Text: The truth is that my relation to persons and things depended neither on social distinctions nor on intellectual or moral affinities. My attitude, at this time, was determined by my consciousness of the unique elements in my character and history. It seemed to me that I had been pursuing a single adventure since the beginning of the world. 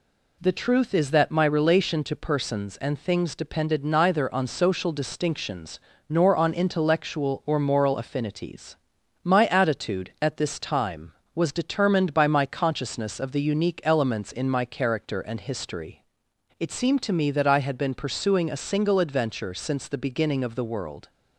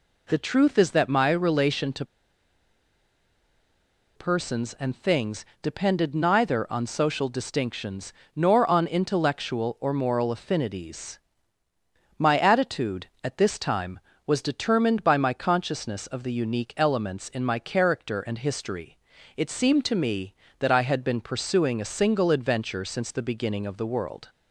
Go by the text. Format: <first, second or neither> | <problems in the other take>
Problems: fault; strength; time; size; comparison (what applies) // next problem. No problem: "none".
first | pauses between "to" and "persons"; strong; at 2.0 s; 2.1 s long // pauses between "things" and "depended"; slight; at 5.4 s; 0.16 s long // pauses between "distinctions" and "nor"; slight; at 8.1 s; 0.22 s long; slight in the first